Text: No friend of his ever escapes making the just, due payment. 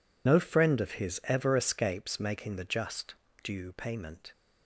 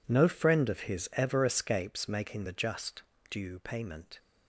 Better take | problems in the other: second | loses the start of "No"; at 0.2 s; 95 ms

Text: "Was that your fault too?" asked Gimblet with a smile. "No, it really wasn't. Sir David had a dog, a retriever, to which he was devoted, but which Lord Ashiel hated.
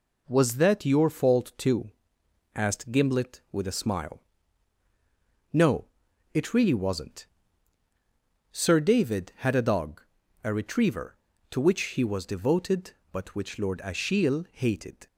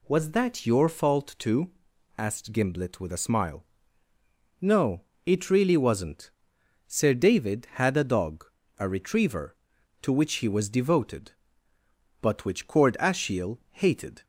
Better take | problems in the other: first | says "Cord" for "Lord"; at 12.6 s

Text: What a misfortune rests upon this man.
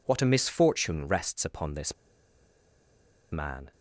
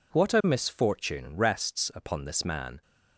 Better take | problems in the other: second | pauses between "this" and "man"; strong; at 1.9 s; 1.3 s long

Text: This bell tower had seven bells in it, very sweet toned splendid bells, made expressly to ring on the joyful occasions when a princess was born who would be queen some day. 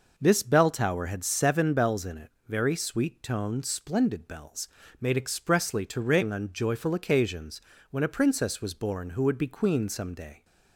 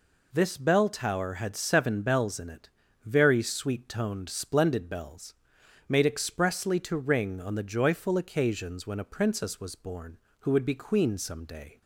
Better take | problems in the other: second | skips "the"; at 6.5 s // pauses between "occasions" and "when"; slight; at 7.6 s; 0.30 s long

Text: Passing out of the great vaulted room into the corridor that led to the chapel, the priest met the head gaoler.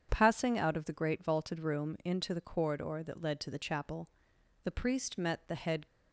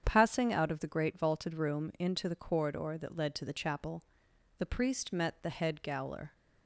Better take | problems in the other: second | starts louder than the rest; strong; until 1.1 s; 7.5 dB; strong in the second // stops before "gaoler"; at 5.8 s

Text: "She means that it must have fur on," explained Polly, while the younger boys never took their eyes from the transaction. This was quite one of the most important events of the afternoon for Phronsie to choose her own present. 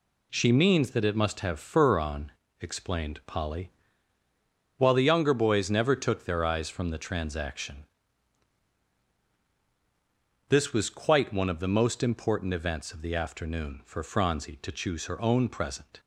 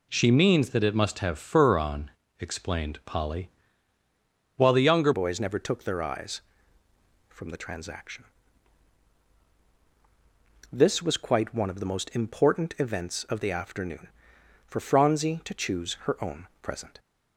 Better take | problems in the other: first | changes voice at "boys"; from 5.1 s on; 11.8 s long // pauses between "own" and "present"; slight; at 16.4 s; 0.16 s long

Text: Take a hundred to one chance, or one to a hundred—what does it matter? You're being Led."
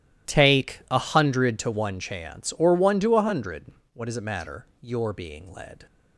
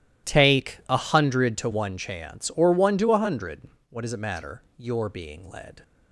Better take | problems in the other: neither | none

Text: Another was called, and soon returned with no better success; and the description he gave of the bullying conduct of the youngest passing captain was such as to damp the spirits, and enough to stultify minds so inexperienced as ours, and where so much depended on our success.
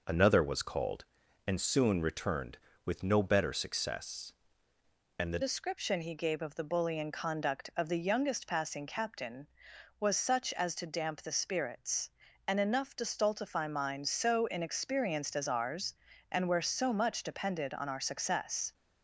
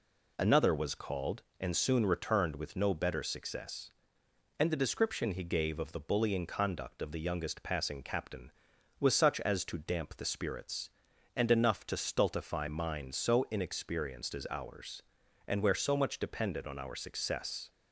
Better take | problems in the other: second | changes voice at "description"; from 5.4 s on; 13.3 s long

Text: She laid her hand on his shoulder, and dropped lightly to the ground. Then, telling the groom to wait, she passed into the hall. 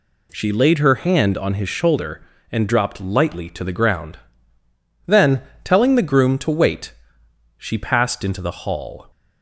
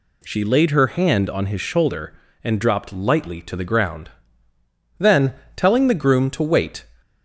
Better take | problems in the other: first | stops before "she passed into the hall"; at 7.0 s

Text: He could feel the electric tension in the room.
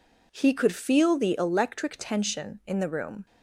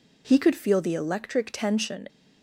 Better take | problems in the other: first | stops before "in the room"; at 2.0 s

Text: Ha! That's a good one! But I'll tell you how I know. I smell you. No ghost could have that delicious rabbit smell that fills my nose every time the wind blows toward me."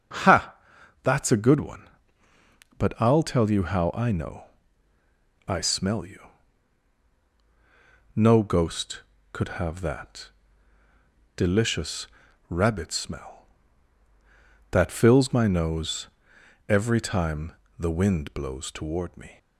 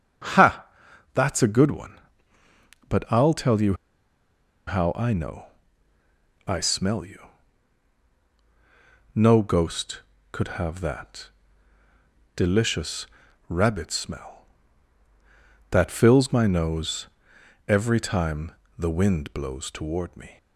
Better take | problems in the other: first | starts louder than the rest; until 1.7 s; 7 dB; also in the first // pauses between "you" and "how"; noticeable; at 3.7 s; 0.92 s long // pauses between "that" and "delicious"; at 11.2 s; 1.0 s long; also in the first // pauses between "delicious" and "rabbit"; at 13.0 s; 0.42 s long; also in the first // pauses between "nose" and "every"; noticeable; at 17.0 s; 0.60 s long; noticeable in the first // pauses between "time" and "the"; slight; at 18.5 s; 0.26 s long; slight in the first

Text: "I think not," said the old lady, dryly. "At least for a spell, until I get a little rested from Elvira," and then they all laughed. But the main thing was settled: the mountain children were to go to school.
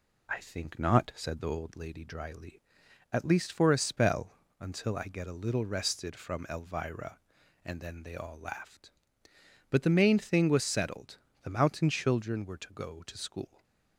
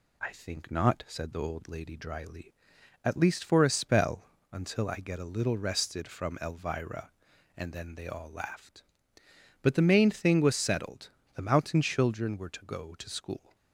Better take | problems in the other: second | starts louder than the rest; slight; until 1.7 s; 2.5 dB // stays silent after the last word; slight; from 13.4 s on; 0.5 s long

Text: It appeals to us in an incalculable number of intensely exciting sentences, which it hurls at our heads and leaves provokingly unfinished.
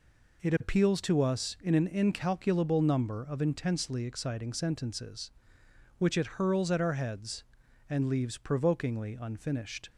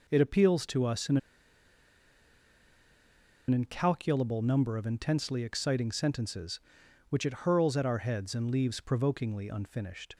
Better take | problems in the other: first | pauses between "in" and "an"; strong; at 1.1 s; 2.3 s long

